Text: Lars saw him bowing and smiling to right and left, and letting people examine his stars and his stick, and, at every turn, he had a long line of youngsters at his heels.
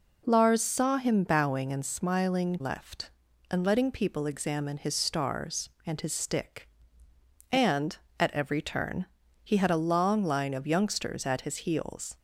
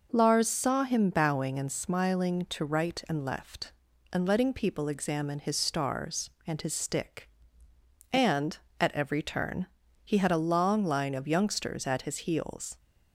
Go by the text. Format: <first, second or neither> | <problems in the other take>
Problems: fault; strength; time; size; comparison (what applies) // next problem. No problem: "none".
second | skips "to right and"; at 2.6 s